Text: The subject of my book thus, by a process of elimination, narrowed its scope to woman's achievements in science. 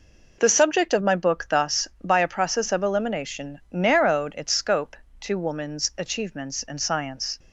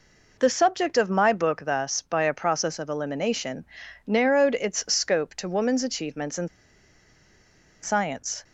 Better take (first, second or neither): first